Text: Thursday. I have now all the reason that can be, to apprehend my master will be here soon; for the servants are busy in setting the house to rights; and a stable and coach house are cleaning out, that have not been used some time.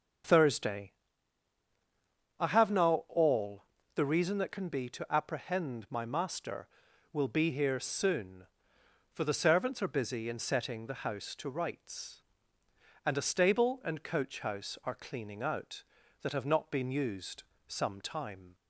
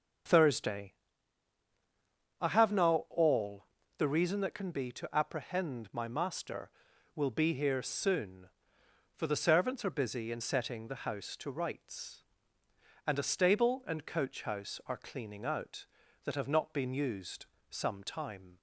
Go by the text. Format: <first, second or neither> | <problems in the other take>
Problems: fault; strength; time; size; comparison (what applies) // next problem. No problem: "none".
neither | starts louder than the rest; the same in both // pauses between "all" and "the"; slight; the same in both // pauses between "used" and "some"; slight; the same in both